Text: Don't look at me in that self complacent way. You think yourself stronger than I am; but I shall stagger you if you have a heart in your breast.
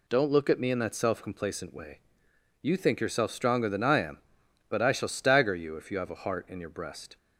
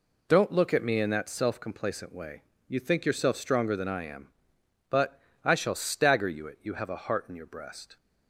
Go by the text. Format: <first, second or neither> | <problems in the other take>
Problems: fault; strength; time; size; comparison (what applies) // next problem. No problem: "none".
first | pauses between "but" and "I"; slight; at 5.2 s; 0.24 s long // says "it" for "if"; at 6.4 s